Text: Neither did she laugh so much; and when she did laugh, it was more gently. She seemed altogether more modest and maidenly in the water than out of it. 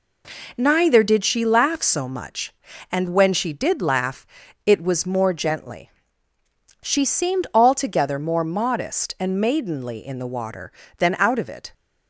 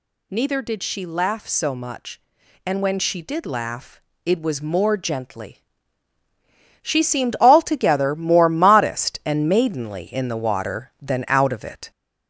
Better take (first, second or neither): first